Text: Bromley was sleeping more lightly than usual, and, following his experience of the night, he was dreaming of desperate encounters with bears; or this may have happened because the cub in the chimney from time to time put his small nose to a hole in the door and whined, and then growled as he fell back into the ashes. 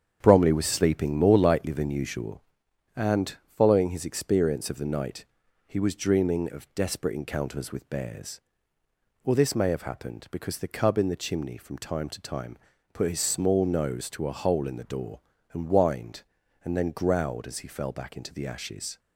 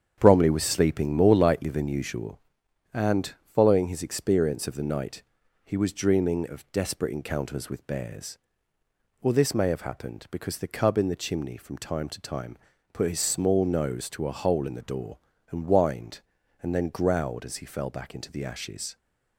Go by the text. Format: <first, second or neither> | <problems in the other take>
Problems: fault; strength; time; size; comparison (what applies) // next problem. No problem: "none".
neither | starts louder than the rest; strong; the same in both // pauses between "time" and "put"; slight; the same in both